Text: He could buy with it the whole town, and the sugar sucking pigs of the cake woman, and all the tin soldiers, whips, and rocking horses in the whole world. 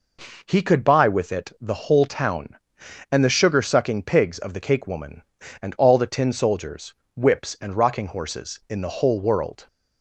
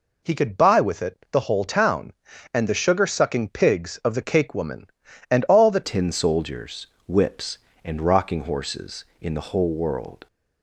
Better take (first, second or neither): first